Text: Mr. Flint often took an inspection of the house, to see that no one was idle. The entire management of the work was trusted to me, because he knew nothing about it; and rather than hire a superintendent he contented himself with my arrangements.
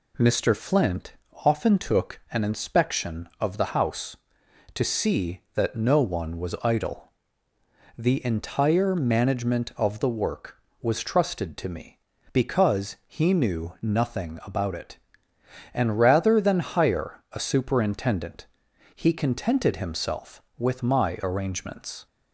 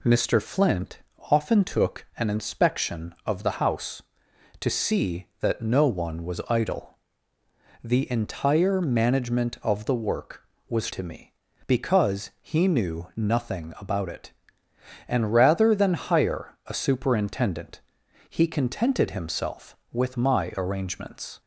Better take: first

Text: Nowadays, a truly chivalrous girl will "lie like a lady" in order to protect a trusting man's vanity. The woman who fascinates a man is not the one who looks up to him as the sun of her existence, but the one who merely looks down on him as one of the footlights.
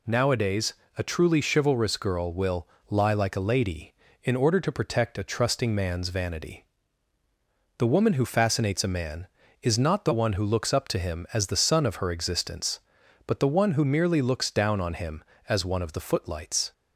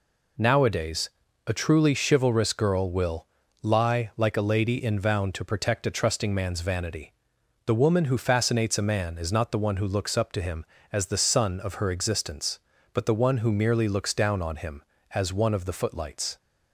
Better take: first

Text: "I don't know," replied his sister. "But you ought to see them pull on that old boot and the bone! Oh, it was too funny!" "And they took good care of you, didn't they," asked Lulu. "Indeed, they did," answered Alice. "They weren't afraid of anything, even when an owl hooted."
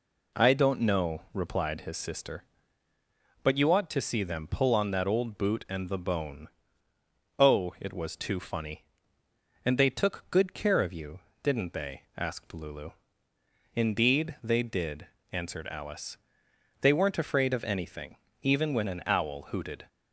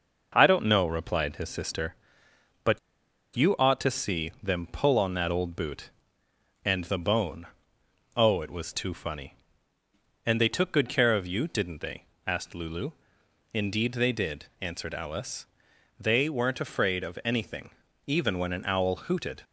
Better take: first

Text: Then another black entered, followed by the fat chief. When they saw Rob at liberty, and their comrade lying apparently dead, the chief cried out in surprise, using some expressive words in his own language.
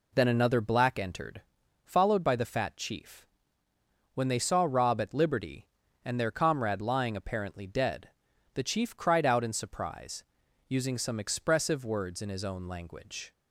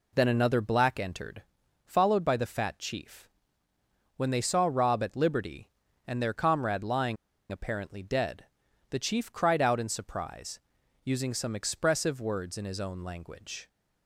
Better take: first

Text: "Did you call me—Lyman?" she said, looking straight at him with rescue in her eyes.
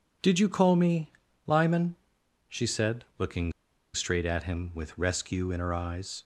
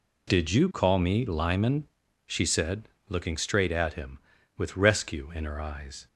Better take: second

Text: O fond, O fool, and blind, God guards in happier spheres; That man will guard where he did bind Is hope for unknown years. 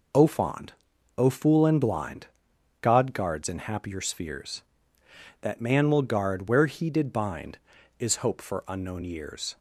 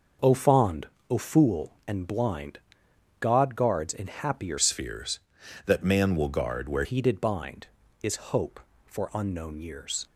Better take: first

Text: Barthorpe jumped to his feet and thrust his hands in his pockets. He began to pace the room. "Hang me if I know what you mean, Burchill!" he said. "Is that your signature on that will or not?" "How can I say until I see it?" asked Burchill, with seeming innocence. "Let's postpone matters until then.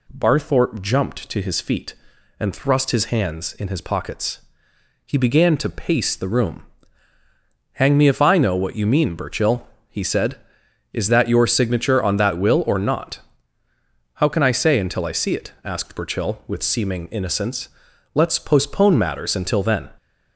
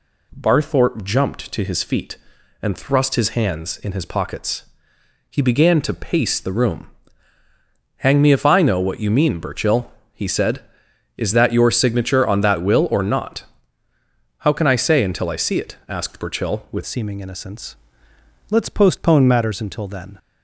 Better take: first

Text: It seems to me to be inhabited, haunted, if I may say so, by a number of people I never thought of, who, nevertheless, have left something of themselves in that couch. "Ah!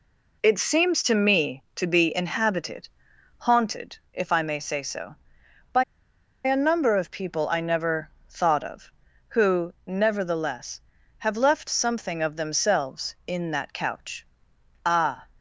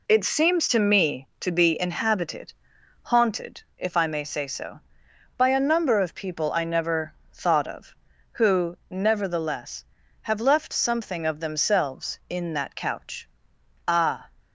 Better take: second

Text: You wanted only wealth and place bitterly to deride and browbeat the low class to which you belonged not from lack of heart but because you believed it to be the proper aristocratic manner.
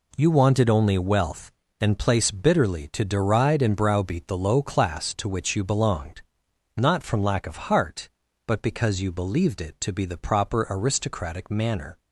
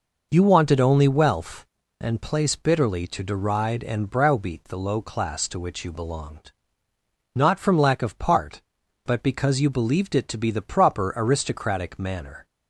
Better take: first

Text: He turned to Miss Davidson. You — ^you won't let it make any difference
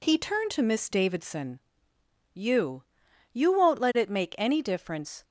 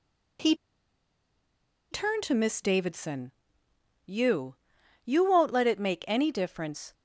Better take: first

